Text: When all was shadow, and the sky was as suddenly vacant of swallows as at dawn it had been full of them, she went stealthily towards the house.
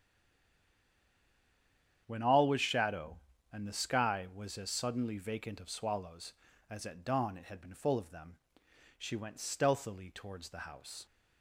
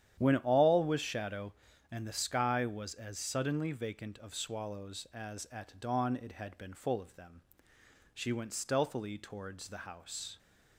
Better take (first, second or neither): second